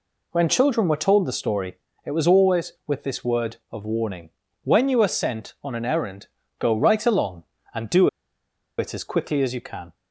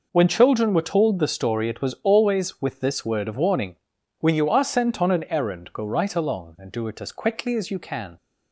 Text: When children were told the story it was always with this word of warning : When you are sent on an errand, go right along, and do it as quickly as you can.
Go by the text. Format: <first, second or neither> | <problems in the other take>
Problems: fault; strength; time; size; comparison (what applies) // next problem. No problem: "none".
second | pauses between "story" and "it"; slight; at 1.7 s; 0.30 s long // pauses between "do" and "it"; noticeable; at 8.0 s; 0.70 s long